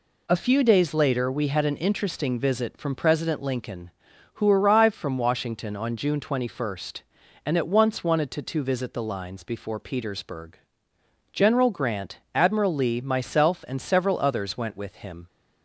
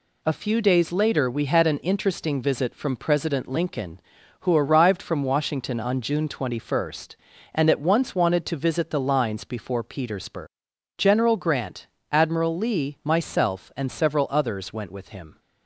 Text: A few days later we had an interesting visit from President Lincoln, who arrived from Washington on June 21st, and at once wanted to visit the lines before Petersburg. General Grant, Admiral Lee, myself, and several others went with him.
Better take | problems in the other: second | says "to" twice; at 8.4 s

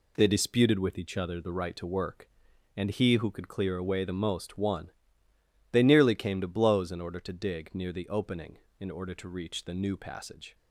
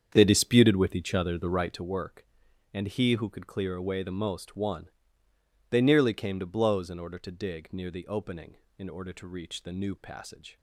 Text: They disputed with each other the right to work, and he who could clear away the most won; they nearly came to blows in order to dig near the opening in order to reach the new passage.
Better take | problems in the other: first | starts louder than the rest; strong; until 1.9 s; 8 dB

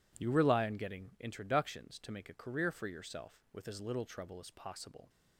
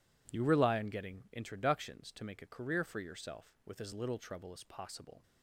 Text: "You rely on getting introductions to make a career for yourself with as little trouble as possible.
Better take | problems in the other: neither | none

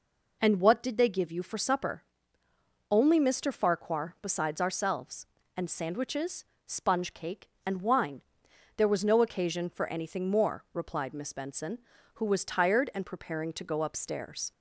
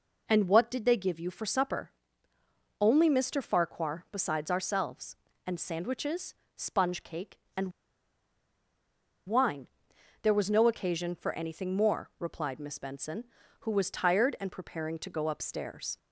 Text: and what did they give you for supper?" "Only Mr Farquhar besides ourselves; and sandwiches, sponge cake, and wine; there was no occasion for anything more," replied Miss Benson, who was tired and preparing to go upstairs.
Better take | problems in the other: first | pauses between "and" and "wine"; strong; at 7.7 s; 1.5 s long

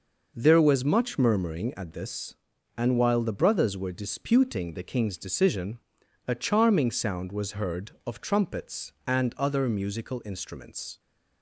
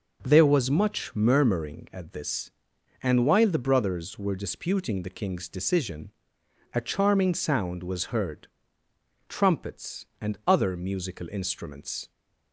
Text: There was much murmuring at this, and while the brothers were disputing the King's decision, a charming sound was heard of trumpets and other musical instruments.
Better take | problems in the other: first | skips "of"; at 8.8 s

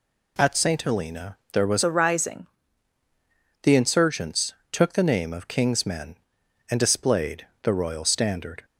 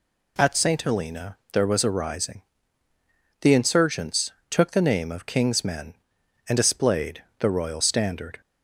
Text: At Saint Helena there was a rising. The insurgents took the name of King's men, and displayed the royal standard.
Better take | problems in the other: second | pauses between "Helena" and "there"; slight; at 1.3 s; 0.16 s long; slight in the second // changes voice from "a" to "rising"; from 1.8 to 2.4 s; 0.6 s long // pauses between "insurgents" and "took"; slight; at 4.5 s; 0.20 s long; slight in the second // pauses between "displayed" and "the"; slight; at 7.4 s; 0.16 s long; slight in the second

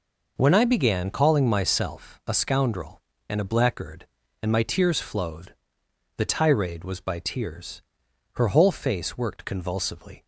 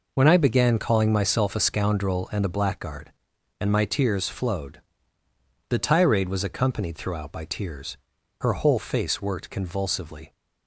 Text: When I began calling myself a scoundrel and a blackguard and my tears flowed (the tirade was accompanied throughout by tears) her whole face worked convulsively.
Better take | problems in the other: second | skips "accompanied throughout"; at 6.9 s

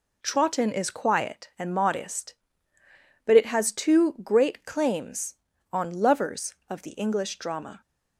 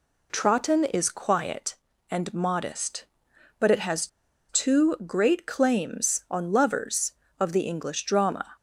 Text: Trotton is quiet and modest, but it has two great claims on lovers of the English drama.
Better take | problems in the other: first | pauses between "has" and "two"; at 4.0 s; 0.42 s long

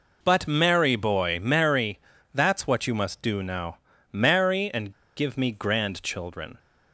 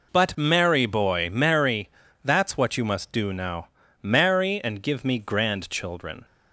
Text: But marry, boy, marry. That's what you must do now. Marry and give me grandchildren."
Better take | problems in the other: second | pauses between "and" and "give"; slight; at 4.9 s; 0.24 s long

